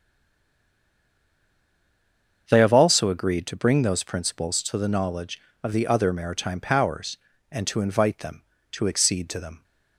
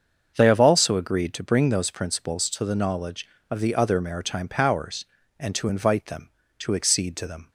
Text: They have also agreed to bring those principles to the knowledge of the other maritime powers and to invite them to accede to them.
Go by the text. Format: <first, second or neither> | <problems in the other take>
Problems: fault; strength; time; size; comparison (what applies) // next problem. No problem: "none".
second | stays silent before the first word; until 2.4 s; 2.4 s long // starts louder than the rest; until 3.5 s; 7 dB; also in the second